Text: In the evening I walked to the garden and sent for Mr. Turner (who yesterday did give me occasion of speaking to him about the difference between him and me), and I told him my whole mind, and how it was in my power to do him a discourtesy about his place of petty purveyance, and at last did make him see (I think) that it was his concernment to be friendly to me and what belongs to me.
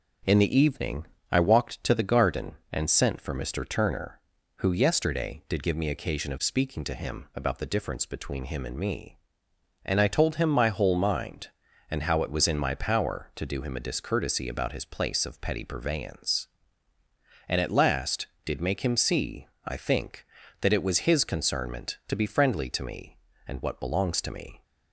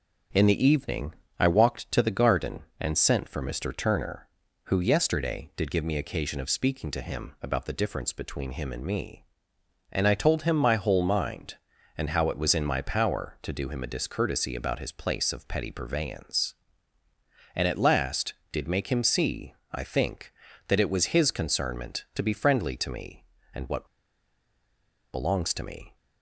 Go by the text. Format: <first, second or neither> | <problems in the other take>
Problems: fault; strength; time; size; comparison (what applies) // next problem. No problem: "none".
first | pauses between "evening" and "I"; slight; at 1.1 s; 0.24 s long; slight in the first // pauses between "what" and "belongs"; strong; at 23.8 s; 1.2 s long